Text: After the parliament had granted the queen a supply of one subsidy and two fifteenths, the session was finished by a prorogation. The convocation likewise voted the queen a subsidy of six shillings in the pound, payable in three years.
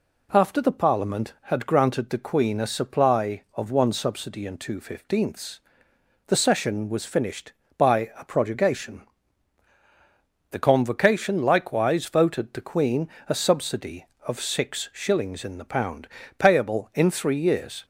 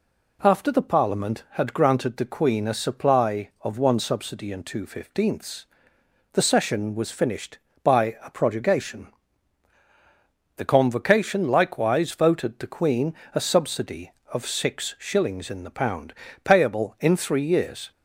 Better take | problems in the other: neither | pauses between "queen" and "a"; slight; the same in both

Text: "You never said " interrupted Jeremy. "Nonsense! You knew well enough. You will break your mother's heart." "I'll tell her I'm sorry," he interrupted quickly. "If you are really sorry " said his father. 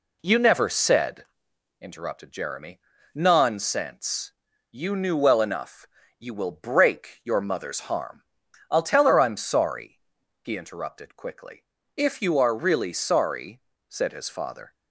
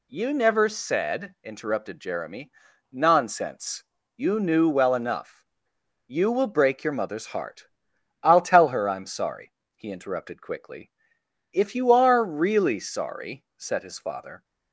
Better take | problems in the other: second | says "harm" for "heart"; at 7.8 s

